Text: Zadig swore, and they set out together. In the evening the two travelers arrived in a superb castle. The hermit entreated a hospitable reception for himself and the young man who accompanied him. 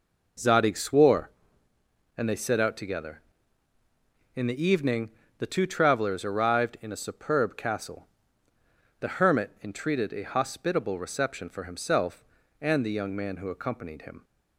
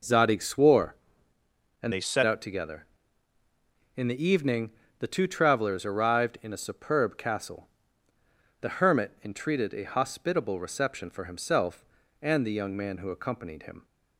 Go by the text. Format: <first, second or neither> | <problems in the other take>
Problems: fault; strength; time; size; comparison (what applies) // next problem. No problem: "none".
first | changes voice from "they" to "set"; from 1.9 to 2.2 s; 0.3 s long // pauses between "evening" and "the"; slight; at 4.7 s; 0.28 s long; slight in the first